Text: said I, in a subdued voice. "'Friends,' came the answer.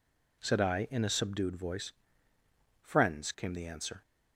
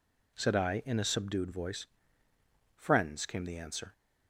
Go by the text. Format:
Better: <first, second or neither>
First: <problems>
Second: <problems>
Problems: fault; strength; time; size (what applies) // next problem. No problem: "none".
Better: neither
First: none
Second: none